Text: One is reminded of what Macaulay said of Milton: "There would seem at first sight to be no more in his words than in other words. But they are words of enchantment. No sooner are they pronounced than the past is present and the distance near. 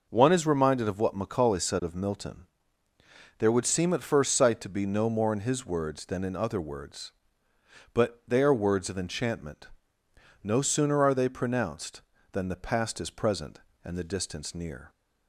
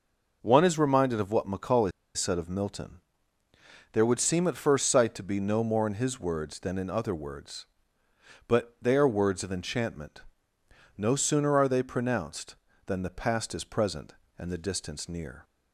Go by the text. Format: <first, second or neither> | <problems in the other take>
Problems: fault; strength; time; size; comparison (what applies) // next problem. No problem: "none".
first | pauses between "Macaulay" and "said"; slight; at 1.9 s; 0.24 s long